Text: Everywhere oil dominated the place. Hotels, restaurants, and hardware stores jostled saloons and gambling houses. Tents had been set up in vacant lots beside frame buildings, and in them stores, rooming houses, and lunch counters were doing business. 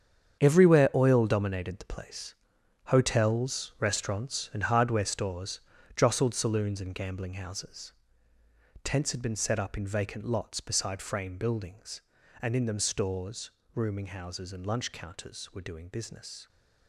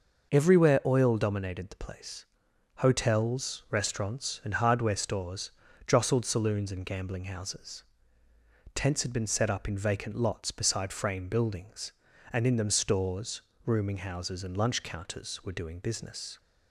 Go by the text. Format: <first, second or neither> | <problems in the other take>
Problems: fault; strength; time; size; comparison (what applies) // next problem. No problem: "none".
second | gets quieter; strong; throughout; 12 dB // pauses between "stores" and "jostled"; slight; at 5.6 s; 0.36 s long; slight in the second